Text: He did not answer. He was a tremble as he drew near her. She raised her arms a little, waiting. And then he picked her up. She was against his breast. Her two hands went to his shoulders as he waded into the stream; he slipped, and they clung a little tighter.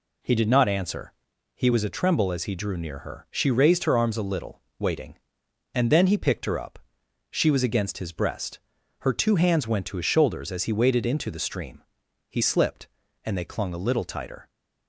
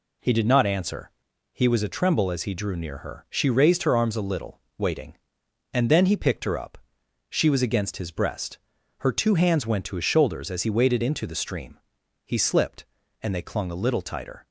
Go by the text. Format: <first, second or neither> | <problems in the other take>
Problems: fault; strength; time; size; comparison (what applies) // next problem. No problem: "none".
neither | none